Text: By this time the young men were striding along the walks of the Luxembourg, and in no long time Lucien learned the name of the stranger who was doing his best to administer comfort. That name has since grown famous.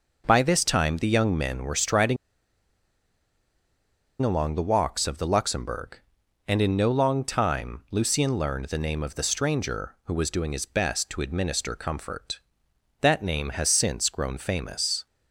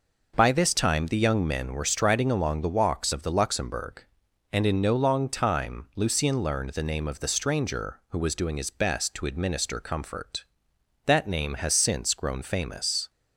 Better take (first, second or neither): second